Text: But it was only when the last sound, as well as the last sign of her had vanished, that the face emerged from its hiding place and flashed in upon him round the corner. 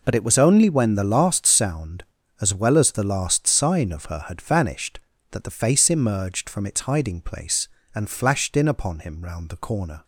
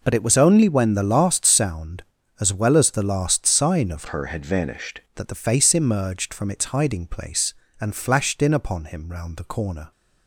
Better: first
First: none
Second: changes voice from "her" to "vanished"; from 4.0 to 5.0 s; 1.0 s long

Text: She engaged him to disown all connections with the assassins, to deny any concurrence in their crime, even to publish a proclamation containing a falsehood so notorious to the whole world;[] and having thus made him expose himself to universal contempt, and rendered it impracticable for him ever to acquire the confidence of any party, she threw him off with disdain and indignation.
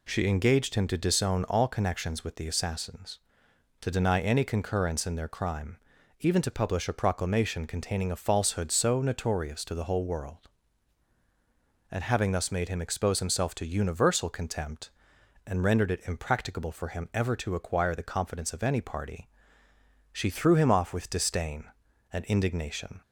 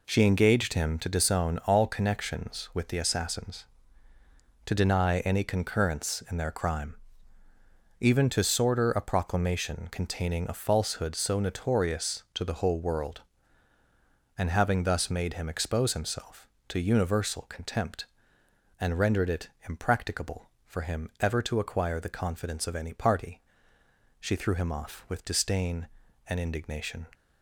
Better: first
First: none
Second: says "sorter" for "publish"; at 8.4 s // pauses between "it" and "impracticable"; slight; at 19.4 s; 0.20 s long

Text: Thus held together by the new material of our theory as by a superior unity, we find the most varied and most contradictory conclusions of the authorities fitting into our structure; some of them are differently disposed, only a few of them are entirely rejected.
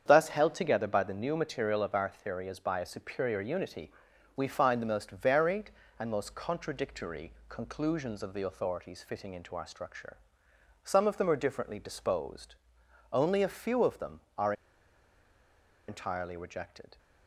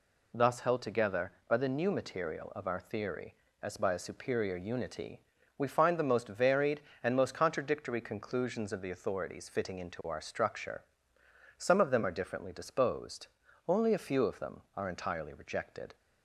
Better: second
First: starts louder than the rest; strong; until 1.0 s; 8 dB // pauses between "contradictory" and "conclusions"; slight; at 7.3 s; 0.16 s long // pauses between "are" and "entirely"; strong; at 14.5 s; 1.3 s long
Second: none

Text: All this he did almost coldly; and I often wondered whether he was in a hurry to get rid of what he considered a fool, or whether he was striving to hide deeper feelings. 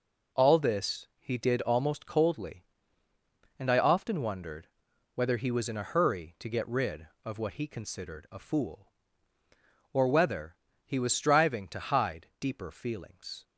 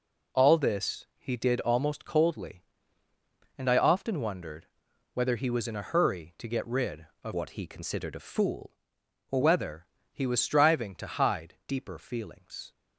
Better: first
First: pauses between "wondered" and "whether"; noticeable; at 4.6 s; 0.48 s long // pauses between "whether" and "he"; slight; at 10.5 s; 0.27 s long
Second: pauses between "wondered" and "whether"; noticeable; at 4.6 s; 0.48 s long // changes voice from "what" to "or"; from 7.3 to 9.4 s; 2.1 s long // pauses between "whether" and "he"; slight; at 9.8 s; 0.24 s long

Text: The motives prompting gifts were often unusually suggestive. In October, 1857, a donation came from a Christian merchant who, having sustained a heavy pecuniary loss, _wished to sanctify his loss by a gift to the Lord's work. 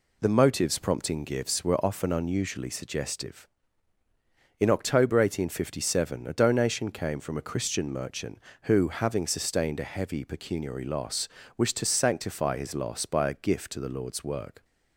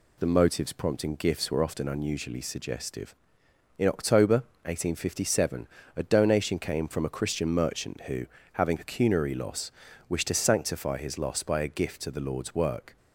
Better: first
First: none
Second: skips "sustained a heavy"; at 8.7 s

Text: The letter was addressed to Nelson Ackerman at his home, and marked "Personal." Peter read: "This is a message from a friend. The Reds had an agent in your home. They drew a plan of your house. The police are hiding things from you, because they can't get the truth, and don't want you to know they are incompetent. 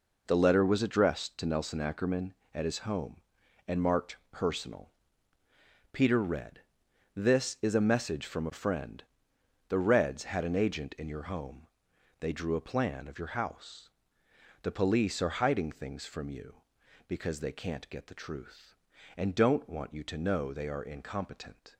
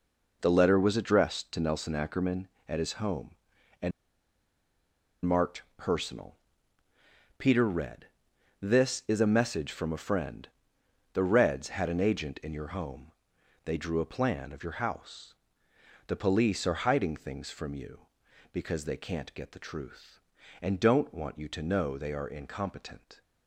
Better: first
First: pauses between "marked" and "Personal"; slight; at 4.1 s; 0.16 s long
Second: pauses between "and" and "marked"; strong; at 3.9 s; 1.3 s long // pauses between "marked" and "Personal"; slight; at 5.6 s; 0.16 s long

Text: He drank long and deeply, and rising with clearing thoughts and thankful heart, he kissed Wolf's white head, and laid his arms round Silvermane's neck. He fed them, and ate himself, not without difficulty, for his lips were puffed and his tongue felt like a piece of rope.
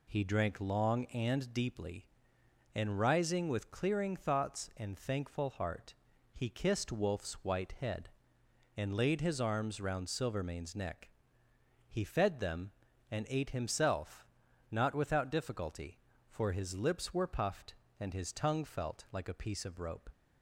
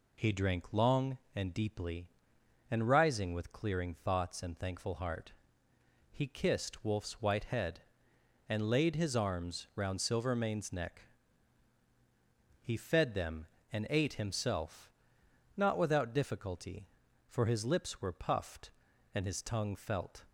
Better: first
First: none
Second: stops before "like a piece of rope"; at 20.2 s

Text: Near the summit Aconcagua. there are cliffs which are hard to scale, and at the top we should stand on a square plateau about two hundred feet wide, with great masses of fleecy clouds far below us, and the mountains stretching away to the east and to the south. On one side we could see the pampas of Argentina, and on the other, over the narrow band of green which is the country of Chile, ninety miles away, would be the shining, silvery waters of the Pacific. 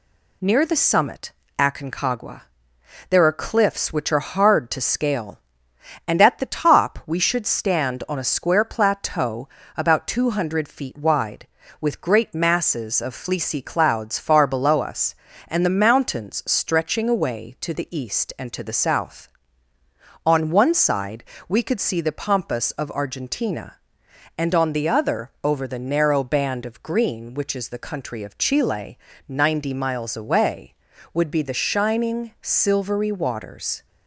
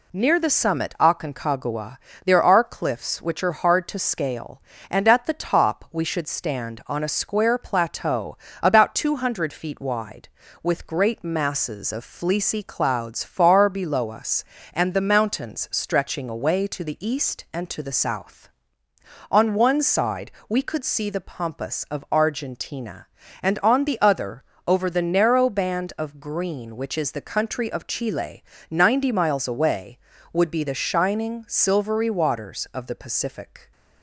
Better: second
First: pauses between "summit" and "Aconcagua"; slight; at 1.3 s; 0.26 s long // pauses between "plateau" and "about"; slight; at 9.4 s; 0.30 s long // pauses between "side" and "we"; slight; at 21.2 s; 0.24 s long // stops before "of the Pacific"; at 33.8 s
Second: pauses between "plateau" and "about"; slight; at 8.3 s; 0.24 s long // pauses between "side" and "we"; slight; at 20.3 s; 0.16 s long

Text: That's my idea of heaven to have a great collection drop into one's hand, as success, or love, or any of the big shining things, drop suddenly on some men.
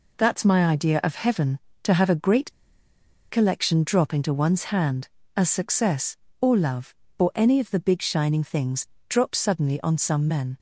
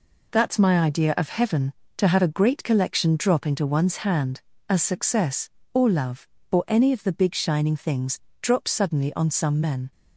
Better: second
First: pauses between "great" and "collection"; noticeable; at 2.5 s; 0.78 s long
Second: none

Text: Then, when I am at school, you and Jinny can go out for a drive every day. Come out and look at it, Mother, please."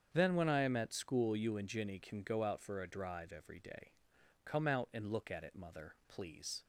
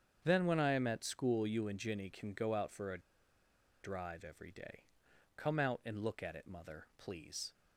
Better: first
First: starts louder than the rest; strong; until 1.1 s; 7.5 dB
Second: starts louder than the rest; strong; until 1.2 s; 7.5 dB // pauses between "a" and "drive"; noticeable; at 3.0 s; 0.82 s long

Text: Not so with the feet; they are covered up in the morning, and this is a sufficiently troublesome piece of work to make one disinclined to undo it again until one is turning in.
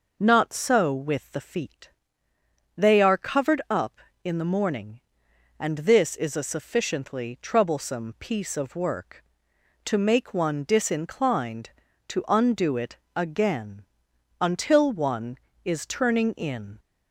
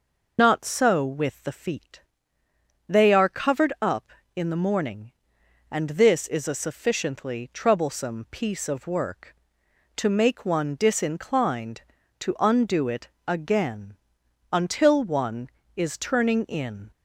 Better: first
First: pauses between "it" and "again"; slight; at 12.9 s; 0.20 s long // pauses between "again" and "until"; noticeable; at 13.8 s; 0.54 s long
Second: loses the start of "Not"; at 0.3 s; 75 ms // pauses between "it" and "again"; slight; at 13.0 s; 0.20 s long // pauses between "again" and "until"; noticeable; at 13.9 s; 0.54 s long

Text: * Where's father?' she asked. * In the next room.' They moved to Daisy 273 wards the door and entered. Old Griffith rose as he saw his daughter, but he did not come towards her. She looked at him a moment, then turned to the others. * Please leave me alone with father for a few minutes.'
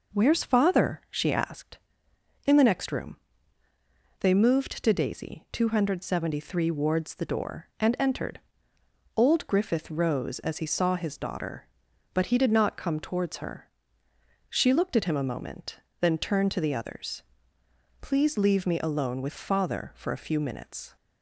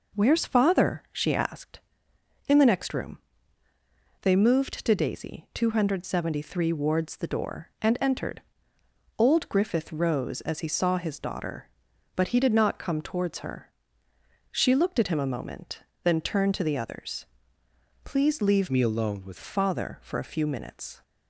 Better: first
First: none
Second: changes voice from "me" to "with"; from 18.6 to 19.3 s; 0.7 s long

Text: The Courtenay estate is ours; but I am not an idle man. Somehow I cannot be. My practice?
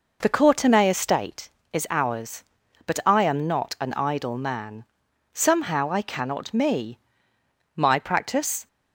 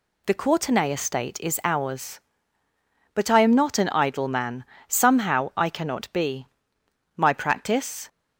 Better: second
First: says "me" for "be"; at 6.5 s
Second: none

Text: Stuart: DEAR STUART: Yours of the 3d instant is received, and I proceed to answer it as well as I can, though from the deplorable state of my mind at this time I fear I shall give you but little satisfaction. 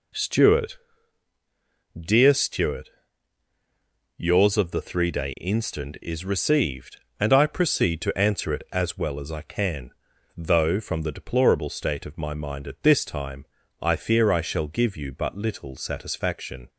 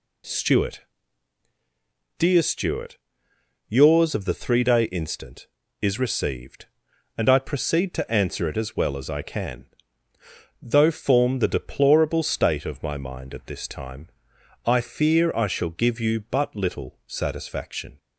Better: first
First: pauses between "time" and "I"; slight; at 13.4 s; 0.36 s long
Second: says "form" for "from"; at 10.9 s // pauses between "time" and "I"; noticeable; at 14.0 s; 0.58 s long

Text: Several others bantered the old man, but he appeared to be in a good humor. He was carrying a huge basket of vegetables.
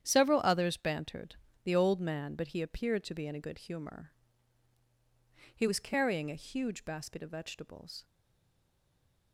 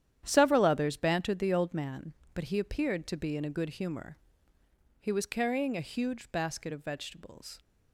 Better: second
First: starts louder than the rest; strong; until 1.0 s; 9.5 dB // pauses between "bantered" and "the"; slight; at 1.3 s; 0.28 s long // stays silent after the last word; noticeable; from 8.0 s on; 1.3 s long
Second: starts louder than the rest; strong; until 1.2 s; 10.5 dB

